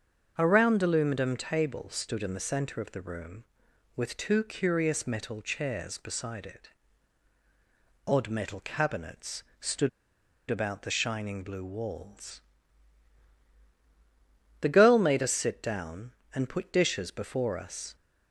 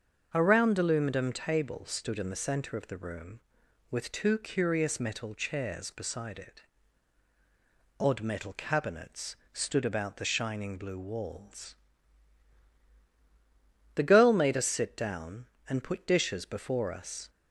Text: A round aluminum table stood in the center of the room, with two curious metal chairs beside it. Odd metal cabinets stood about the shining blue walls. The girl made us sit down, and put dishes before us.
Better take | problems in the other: second | starts louder than the rest; until 1.3 s; 6.5 dB; also in the second // pauses between "cabinets" and "stood"; slight; at 9.4 s; 0.18 s long; slight in the second // pauses between "stood" and "about"; noticeable; at 9.8 s; 0.61 s long

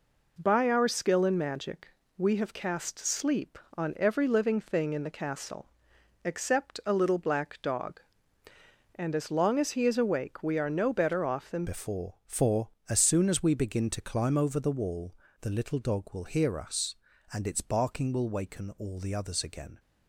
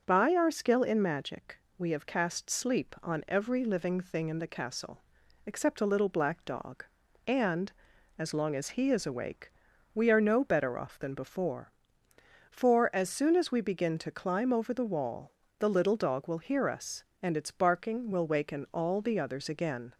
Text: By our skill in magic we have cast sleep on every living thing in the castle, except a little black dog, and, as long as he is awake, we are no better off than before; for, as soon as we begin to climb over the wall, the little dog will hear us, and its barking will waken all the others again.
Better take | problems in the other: second | pauses between "magic" and "we"; slight; at 1.8 s; 0.28 s long; slight in the second // changes voice at "before"; from 11.6 s on; 8.1 s long

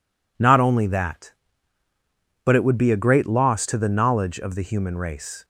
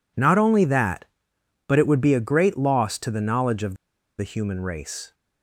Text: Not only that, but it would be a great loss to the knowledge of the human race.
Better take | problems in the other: first | pauses between "of" and "the"; at 3.7 s; 0.43 s long

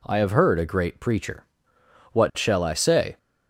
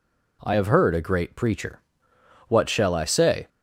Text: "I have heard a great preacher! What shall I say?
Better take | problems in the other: neither | none

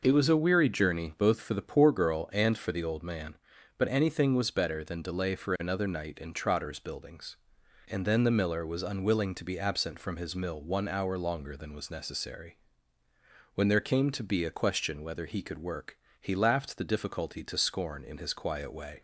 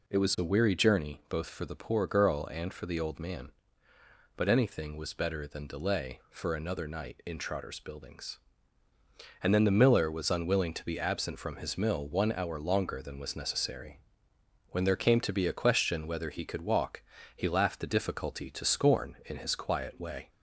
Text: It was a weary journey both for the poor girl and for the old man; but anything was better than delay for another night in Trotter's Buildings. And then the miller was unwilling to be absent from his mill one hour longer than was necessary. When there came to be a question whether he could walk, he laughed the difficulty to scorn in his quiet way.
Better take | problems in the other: second | says "work" for "walk"; at 15.5 s

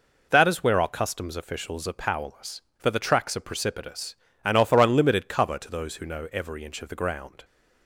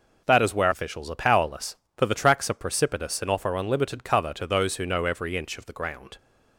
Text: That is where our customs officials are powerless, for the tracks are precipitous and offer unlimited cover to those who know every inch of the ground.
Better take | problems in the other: first | skips "our customs"; at 0.7 s

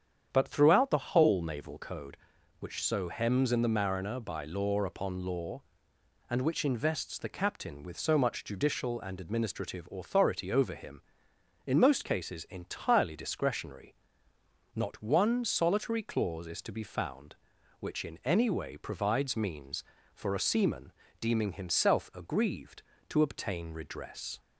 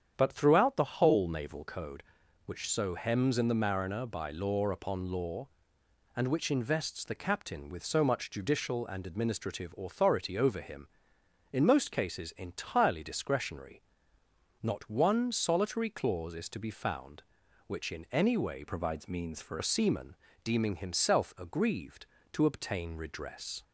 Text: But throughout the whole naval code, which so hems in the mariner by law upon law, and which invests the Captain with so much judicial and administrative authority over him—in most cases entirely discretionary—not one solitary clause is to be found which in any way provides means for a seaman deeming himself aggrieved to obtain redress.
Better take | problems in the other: first | starts louder than the rest; strong; until 1.1 s; 8.5 dB; strong in the first // changes voice from "provides" to "for"; from 18.6 to 19.5 s; 0.9 s long // pauses between "seaman" and "deeming"; slight; at 20.1 s; 0.28 s long; slight in the first

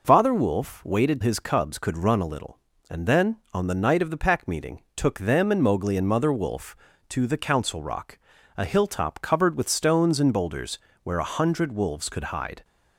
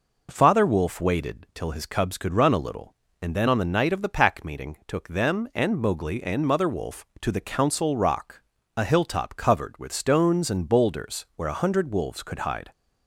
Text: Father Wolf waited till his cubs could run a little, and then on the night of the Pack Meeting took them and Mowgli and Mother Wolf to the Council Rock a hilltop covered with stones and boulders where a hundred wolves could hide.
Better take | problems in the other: second | skips "till"; at 1.2 s // pauses between "Meeting" and "took"; slight; at 4.8 s; 0.16 s long // pauses between "Rock" and "a"; at 8.1 s; 0.40 s long; slight in the second // pauses between "boulders" and "where"; slight; at 10.7 s; 0.24 s long

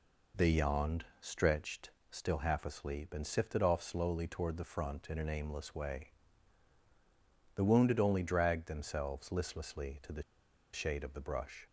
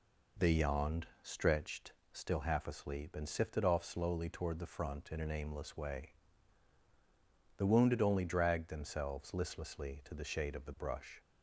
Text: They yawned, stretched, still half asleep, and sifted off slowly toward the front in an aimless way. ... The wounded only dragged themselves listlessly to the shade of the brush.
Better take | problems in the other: second | pauses between "the" and "shade"; noticeable; at 10.2 s; 0.51 s long

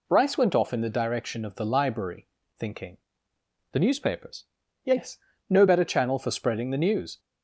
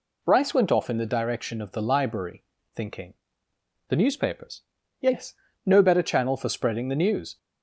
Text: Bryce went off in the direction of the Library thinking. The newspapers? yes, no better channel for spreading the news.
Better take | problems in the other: neither | pauses between "Library" and "thinking"; slight; the same in both

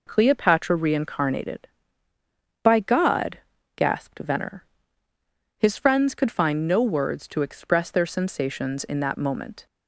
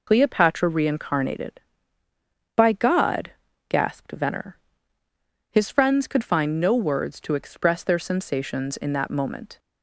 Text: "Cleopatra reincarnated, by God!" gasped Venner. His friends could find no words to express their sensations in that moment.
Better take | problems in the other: first | loses the start of "Cleopatra"; at 0.0 s; 70 ms

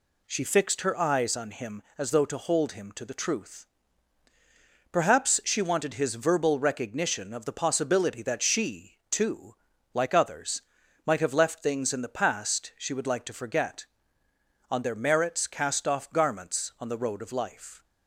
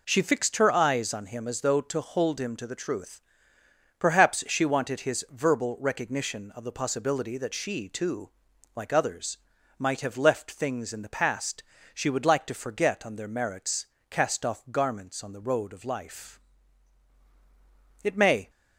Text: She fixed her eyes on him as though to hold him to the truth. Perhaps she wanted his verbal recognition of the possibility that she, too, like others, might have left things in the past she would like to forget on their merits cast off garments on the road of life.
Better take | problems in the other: first | pauses between "past" and "she"; slight; at 11.6 s; 0.30 s long // pauses between "merits" and "cast"; slight; at 13.8 s; 0.22 s long // goes on to say "It may"; slight; from 18.0 s on; 0.46 s long

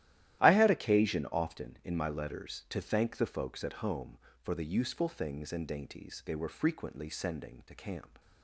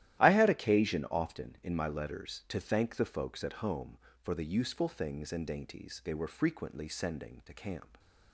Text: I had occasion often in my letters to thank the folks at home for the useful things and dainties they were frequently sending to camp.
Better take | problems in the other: neither | starts louder than the rest; strong; the same in both

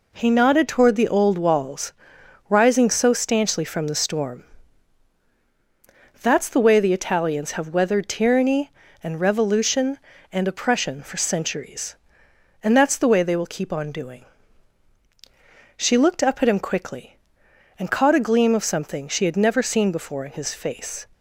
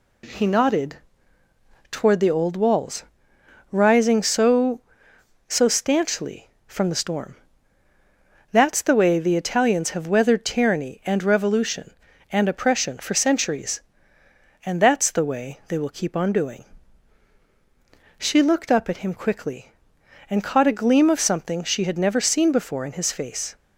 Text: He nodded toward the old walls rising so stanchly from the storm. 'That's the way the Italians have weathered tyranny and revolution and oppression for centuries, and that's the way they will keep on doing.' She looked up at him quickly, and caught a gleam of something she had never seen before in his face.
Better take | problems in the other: first | pauses between "nodded" and "toward"; noticeable; at 0.9 s; 0.94 s long // pauses between "walls" and "rising"; noticeable; at 3.0 s; 0.66 s long; noticeable in the first // says "so" twice; at 5.4 s

